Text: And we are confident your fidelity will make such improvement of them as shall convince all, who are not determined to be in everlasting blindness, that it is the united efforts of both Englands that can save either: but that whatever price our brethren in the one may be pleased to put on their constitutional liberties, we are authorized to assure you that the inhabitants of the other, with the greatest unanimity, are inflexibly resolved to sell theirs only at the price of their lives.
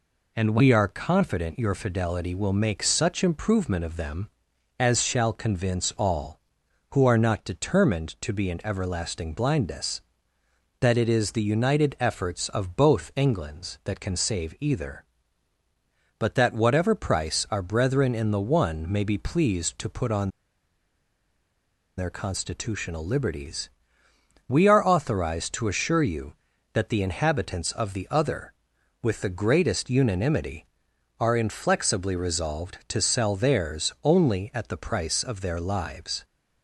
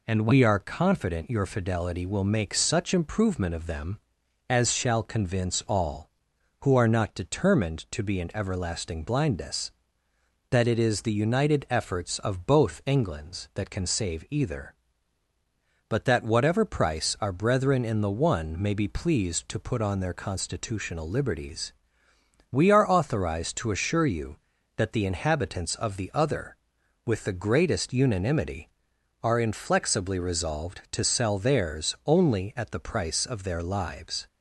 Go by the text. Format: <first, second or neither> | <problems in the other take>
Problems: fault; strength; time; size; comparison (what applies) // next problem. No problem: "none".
second | pauses between "on" and "their"; strong; at 20.2 s; 1.6 s long